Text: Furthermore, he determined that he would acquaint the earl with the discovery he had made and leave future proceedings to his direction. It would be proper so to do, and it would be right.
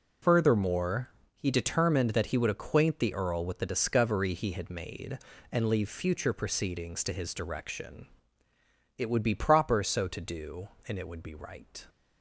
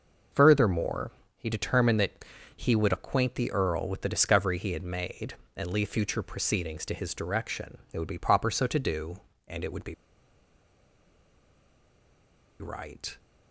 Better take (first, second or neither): first